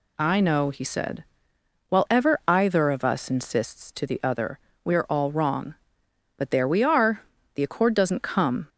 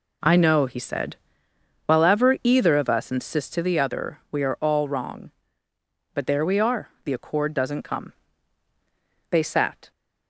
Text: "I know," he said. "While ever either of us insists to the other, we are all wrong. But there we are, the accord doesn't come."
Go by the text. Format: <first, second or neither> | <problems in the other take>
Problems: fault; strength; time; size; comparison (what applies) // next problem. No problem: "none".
first | goes on to say "They sat"; noticeable; from 9.2 s on; 0.62 s long